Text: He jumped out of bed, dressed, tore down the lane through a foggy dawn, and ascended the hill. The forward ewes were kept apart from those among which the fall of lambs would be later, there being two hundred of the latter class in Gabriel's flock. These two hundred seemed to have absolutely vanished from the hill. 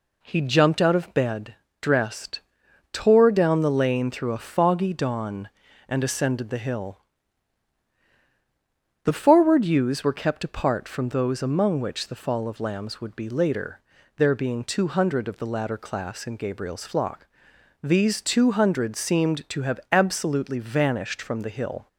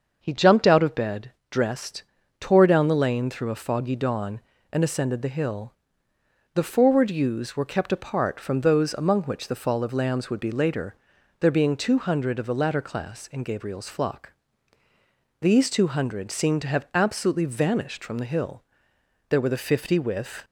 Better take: first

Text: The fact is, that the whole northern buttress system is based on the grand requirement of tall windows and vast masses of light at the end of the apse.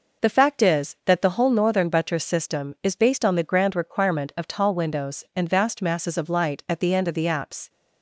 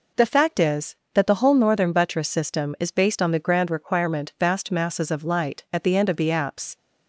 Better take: first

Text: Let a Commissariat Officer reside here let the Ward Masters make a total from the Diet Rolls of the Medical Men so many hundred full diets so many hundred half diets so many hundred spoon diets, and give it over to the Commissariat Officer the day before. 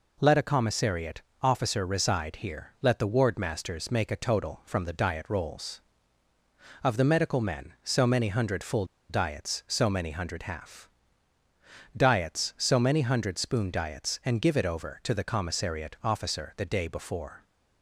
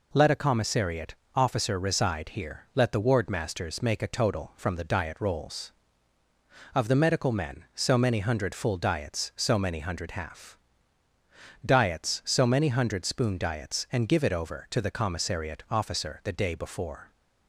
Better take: second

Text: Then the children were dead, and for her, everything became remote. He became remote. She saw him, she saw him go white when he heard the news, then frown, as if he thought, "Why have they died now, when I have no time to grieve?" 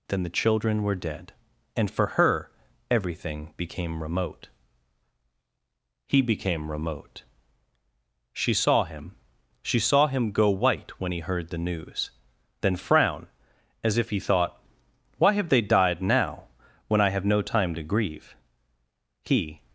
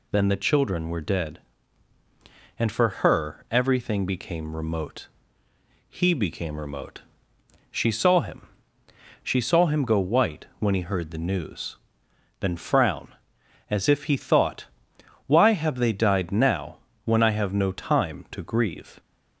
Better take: second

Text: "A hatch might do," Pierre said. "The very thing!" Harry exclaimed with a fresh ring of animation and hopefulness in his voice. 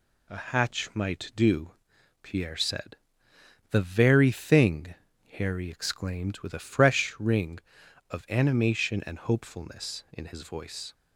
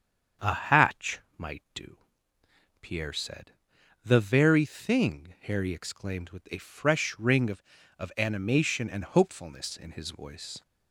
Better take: first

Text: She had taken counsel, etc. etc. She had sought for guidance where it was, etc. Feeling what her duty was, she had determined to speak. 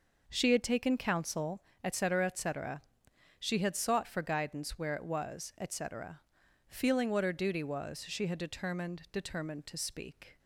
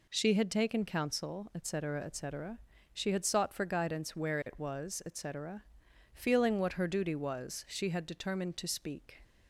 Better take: second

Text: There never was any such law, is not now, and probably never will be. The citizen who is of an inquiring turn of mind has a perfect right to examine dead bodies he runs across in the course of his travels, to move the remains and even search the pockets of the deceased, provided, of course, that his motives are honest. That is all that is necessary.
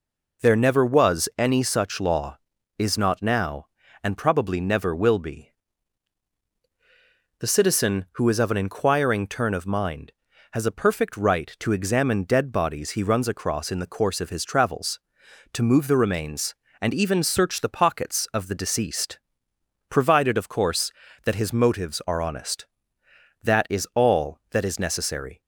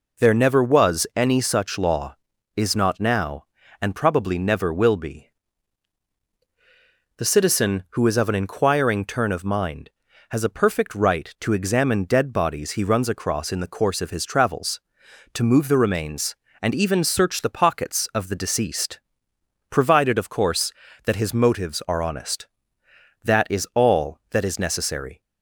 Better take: neither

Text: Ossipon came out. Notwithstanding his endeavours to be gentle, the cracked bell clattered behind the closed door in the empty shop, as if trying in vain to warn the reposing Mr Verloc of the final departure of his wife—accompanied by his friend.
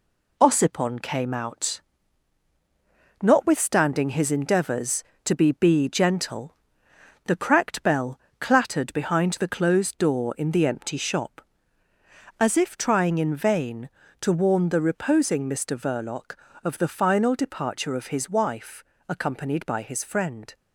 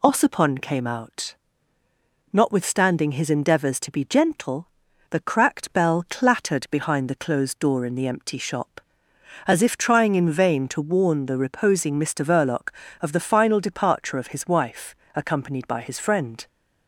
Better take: second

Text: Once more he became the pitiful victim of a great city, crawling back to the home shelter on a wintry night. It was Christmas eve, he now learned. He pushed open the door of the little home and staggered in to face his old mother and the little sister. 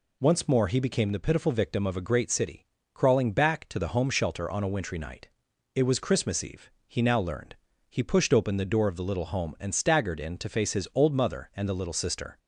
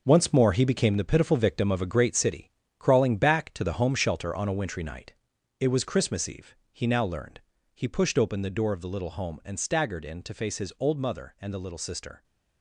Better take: first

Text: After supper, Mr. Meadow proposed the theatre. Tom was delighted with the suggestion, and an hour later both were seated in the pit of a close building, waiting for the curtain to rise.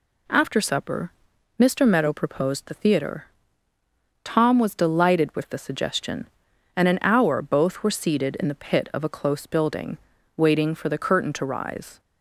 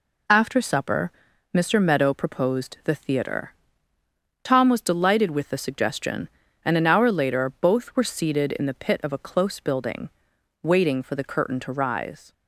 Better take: second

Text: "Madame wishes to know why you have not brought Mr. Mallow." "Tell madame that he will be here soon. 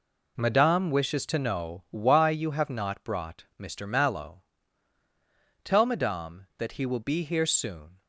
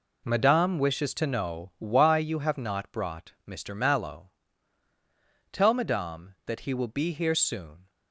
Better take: neither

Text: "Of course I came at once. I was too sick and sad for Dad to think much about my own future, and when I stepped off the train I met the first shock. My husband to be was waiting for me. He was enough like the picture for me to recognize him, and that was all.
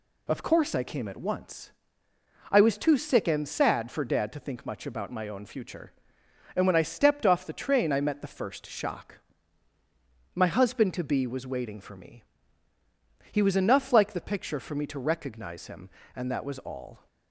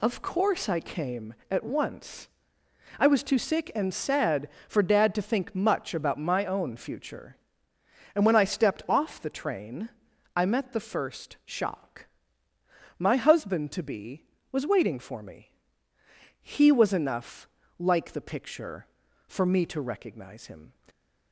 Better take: first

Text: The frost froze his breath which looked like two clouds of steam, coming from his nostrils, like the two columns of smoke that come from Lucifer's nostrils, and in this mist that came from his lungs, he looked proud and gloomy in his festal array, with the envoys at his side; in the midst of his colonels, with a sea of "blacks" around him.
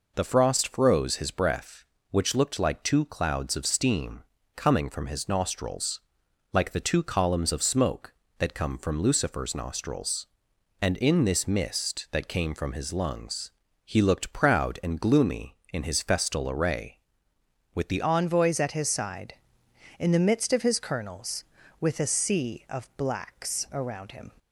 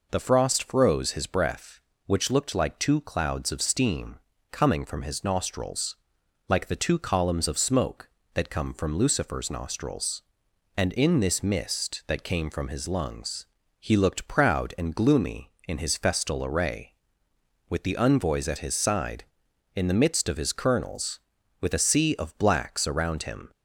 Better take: second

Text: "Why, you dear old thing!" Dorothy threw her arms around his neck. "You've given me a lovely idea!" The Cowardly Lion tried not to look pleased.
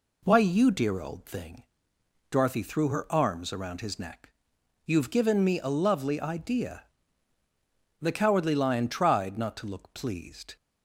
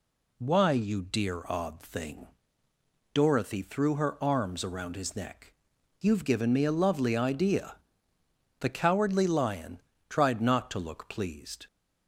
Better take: first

